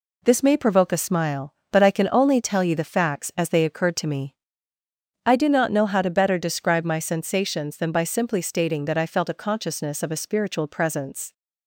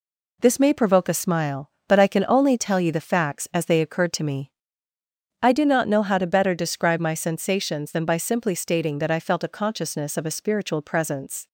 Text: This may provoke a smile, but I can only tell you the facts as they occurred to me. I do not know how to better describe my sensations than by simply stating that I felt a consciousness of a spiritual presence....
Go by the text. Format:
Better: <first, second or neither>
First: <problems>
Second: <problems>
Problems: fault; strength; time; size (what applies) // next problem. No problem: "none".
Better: neither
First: none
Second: none